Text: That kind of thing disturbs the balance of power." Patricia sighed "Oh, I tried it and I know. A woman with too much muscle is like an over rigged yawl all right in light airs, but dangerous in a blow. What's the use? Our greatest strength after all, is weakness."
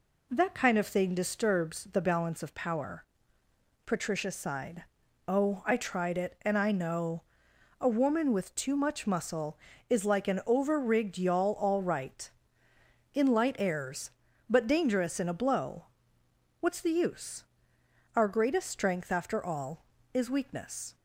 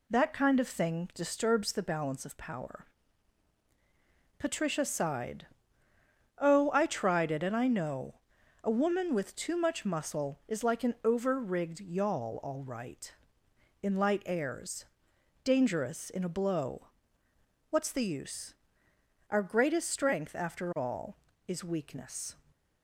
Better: first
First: pauses between "sighed" and "Oh"; at 4.8 s; 0.42 s long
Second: pauses between "sighed" and "Oh"; noticeable; at 5.4 s; 0.90 s long // skips "but"; at 15.1 s

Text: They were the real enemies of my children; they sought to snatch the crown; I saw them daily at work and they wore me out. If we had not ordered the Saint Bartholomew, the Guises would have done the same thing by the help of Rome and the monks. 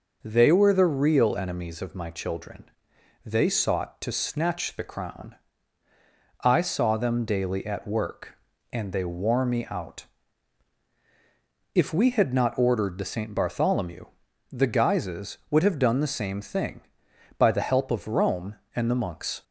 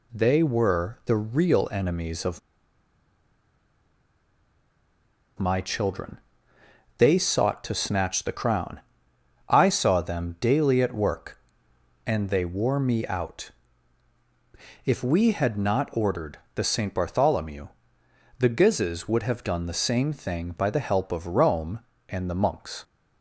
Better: first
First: none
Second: pauses between "of" and "my"; strong; at 2.4 s; 2.9 s long // pauses between "ordered" and "the"; slight; at 16.3 s; 0.18 s long

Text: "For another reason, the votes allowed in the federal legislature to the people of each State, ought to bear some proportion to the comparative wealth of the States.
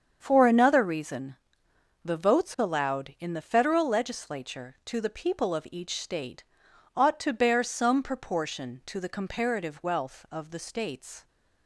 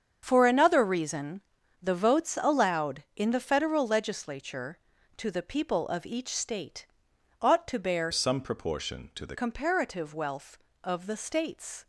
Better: first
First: starts louder than the rest; strong; until 1.2 s; 7.5 dB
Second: starts louder than the rest; until 1.2 s; 7 dB // changes voice from "some" to "the"; from 8.1 to 9.3 s; 1.2 s long

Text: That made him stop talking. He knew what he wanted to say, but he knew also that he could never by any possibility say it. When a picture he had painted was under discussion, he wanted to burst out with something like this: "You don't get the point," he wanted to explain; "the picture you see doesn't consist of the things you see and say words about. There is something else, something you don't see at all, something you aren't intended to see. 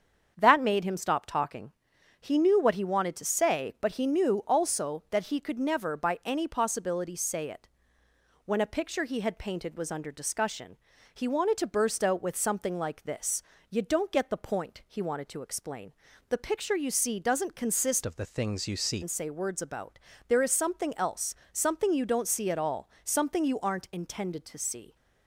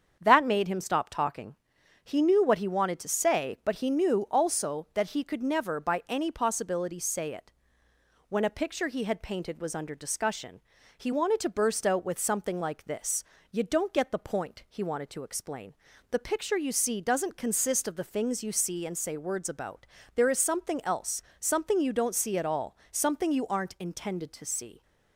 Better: second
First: starts louder than the rest; strong; until 1.3 s; 7.5 dB // changes voice from "of" to "see"; from 18.0 to 19.0 s; 1.0 s long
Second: starts louder than the rest; strong; until 1.2 s; 7 dB

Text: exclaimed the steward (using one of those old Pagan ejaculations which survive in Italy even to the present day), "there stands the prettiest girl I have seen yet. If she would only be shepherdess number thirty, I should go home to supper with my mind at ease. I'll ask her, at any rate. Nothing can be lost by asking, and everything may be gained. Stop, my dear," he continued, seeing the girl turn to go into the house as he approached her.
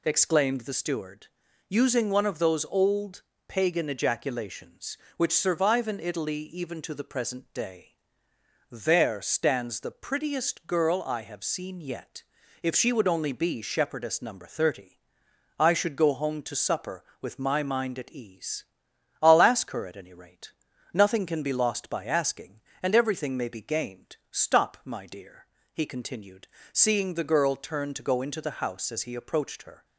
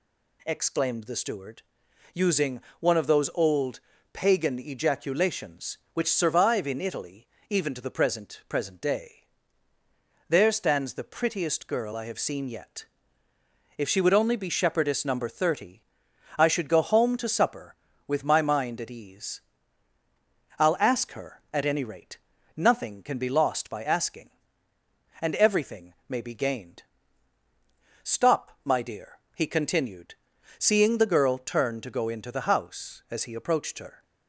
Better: first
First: pauses between "old" and "Pagan"; slight; at 3.2 s; 0.26 s long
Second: pauses between "using" and "one"; slight; at 2.5 s; 0.20 s long // pauses between "old" and "Pagan"; slight; at 3.7 s; 0.32 s long // pauses between "Italy" and "even"; slight; at 7.2 s; 0.20 s long // says "present" twice; at 8.4 s // pauses between "everything" and "may"; slight; at 25.9 s; 0.16 s long

